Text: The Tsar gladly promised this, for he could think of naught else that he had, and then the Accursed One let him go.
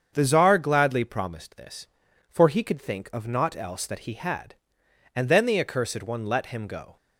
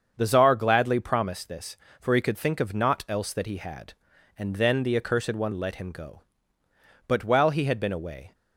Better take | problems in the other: first | starts louder than the rest; until 1.1 s; 7 dB; also in the first // goes on to say "But while he had been away"; noticeable; from 7.0 s on; 1.2 s long

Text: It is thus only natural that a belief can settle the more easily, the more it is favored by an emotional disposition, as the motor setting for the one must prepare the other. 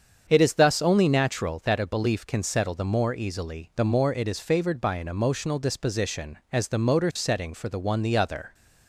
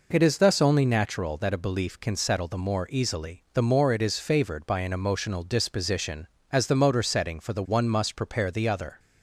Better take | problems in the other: second | starts louder than the rest; strong; until 1.2 s; 7.5 dB // skips "must prepare"; at 8.0 s

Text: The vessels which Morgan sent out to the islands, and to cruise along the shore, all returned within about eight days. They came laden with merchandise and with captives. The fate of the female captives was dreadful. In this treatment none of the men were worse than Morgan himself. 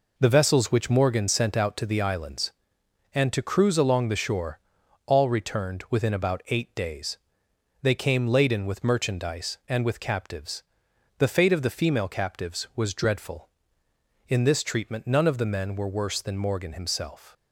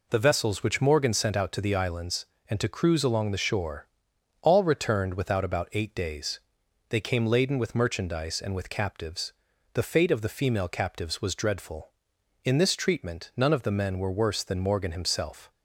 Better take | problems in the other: first | says "without" for "within"; at 5.1 s

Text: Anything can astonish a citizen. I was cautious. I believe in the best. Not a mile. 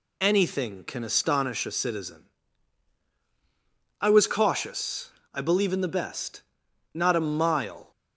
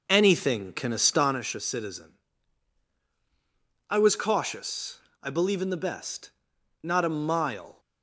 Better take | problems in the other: first | starts louder than the rest; noticeable; until 1.5 s; 5.5 dB

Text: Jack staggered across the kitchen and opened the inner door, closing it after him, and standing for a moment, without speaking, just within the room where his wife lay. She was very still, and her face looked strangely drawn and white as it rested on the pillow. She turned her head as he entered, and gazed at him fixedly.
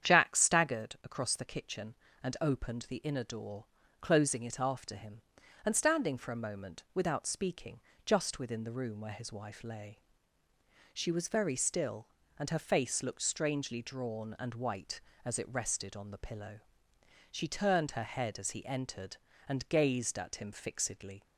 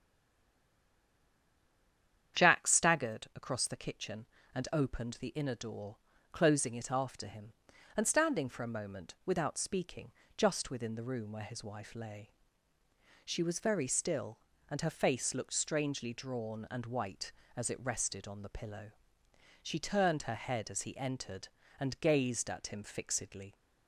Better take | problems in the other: first | stays silent before the first word; until 2.3 s; 2.3 s long // starts louder than the rest; strong; until 3.4 s; 8.5 dB; strong in the first

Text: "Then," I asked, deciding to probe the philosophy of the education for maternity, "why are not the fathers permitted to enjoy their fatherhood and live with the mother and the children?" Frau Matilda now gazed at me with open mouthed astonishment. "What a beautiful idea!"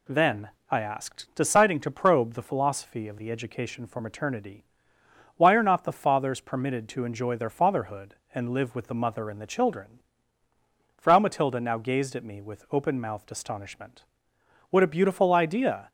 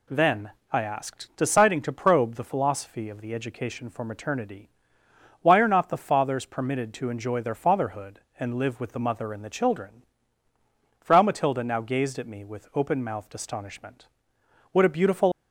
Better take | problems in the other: first | stops before "idea"; at 15.3 s

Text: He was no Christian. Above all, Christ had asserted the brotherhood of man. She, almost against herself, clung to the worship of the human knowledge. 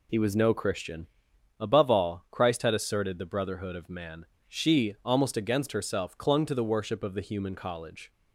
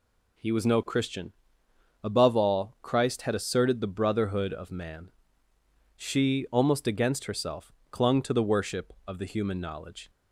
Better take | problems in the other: second | says "college" for "knowledge"; at 7.5 s

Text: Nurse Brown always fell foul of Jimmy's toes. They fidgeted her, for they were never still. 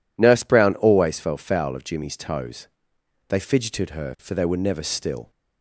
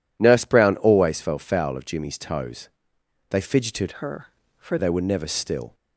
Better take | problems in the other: first | changes voice from "her" to "for"; from 3.9 to 4.7 s; 0.8 s long

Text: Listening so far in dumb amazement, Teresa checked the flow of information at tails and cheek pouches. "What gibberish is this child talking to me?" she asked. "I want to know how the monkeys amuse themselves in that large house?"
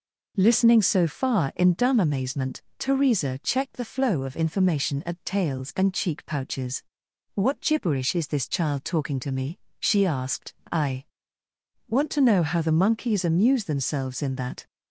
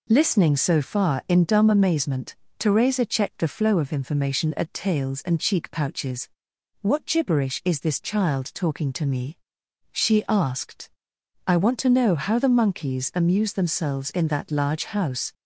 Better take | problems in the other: second | pauses between "I" and "want"; noticeable; at 11.0 s; 0.82 s long // stops before "large house"; at 14.6 s

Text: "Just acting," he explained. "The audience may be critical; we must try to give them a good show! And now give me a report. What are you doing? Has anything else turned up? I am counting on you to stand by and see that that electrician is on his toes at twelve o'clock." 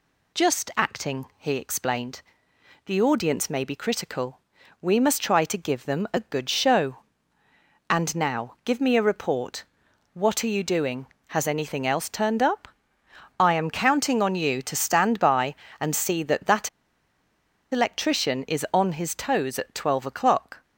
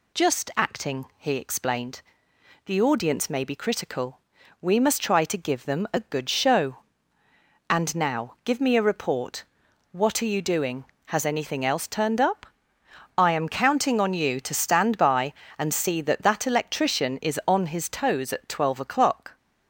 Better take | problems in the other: second | pauses between "that" and "electrician"; at 16.6 s; 1.0 s long

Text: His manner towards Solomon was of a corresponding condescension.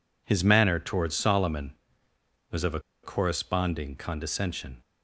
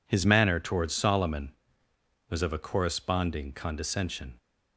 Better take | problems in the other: second | pauses between "a" and "corresponding"; slight; at 2.7 s; 0.24 s long

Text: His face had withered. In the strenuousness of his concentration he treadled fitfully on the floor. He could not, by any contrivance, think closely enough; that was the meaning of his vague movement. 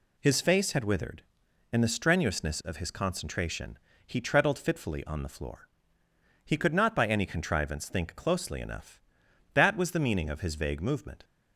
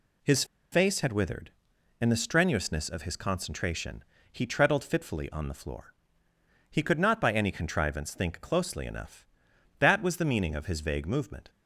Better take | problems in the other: first | pauses between "His" and "face"; slight; at 0.4 s; 0.28 s long // pauses between "concentration" and "he"; slight; at 4.0 s; 0.28 s long; slight in the first

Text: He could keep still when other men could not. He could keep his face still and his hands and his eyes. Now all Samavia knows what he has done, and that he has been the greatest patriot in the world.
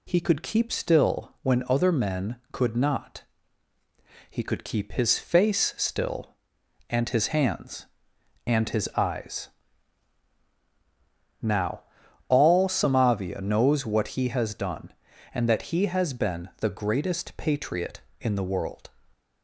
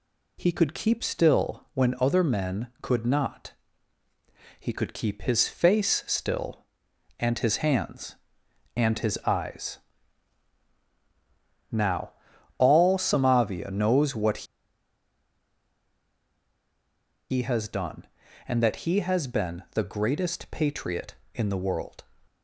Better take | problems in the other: first | pauses between "Now" and "all"; noticeable; at 12.1 s; 0.46 s long; noticeable in the first // pauses between "what" and "he"; strong; at 14.4 s; 2.8 s long

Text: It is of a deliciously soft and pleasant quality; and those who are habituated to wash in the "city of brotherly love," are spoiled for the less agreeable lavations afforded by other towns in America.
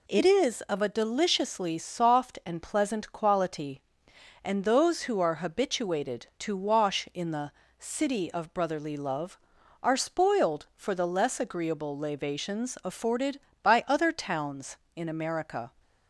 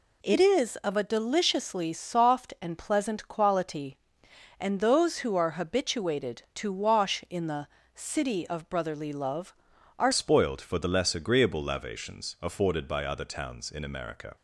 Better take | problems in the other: first | pauses between "the" and "city"; slight; at 7.6 s; 0.28 s long; slight in the first // changes voice at "spoiled"; from 10.1 s on; 4.2 s long

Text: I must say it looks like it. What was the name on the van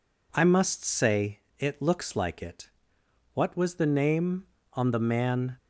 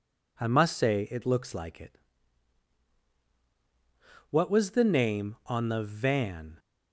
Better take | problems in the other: second | pauses between "say" and "it"; slight; at 1.4 s; 0.18 s long // says "man" for "van"; at 4.9 s

